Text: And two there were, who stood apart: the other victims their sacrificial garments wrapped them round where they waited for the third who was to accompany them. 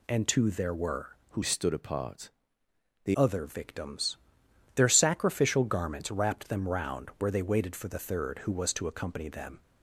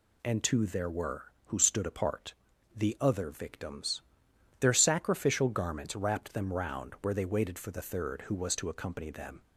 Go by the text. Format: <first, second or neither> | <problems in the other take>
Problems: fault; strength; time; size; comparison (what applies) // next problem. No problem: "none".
second | changes voice from "stood" to "the"; from 1.4 to 3.1 s; 1.7 s long // pauses between "victims" and "their"; noticeable; at 4.1 s; 0.58 s long; noticeable in the second